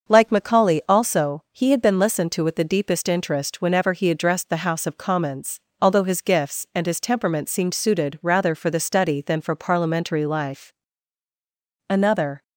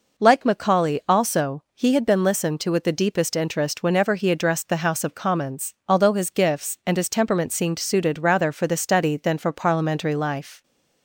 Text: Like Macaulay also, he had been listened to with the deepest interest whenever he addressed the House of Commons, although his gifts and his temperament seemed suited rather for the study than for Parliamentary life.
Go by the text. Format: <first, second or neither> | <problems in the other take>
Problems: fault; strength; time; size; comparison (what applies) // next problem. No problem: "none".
second | starts louder than the rest; until 1.1 s; 6.5 dB // goes on to say "Another"; from 11.9 s on; 0.52 s long